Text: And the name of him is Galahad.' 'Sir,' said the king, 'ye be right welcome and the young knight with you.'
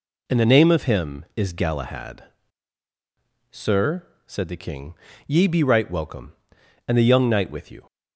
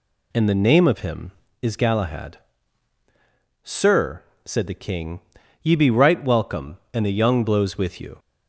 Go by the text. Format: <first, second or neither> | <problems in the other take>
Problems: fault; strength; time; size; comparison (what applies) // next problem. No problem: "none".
first | says "blows" for "knight"; at 7.4 s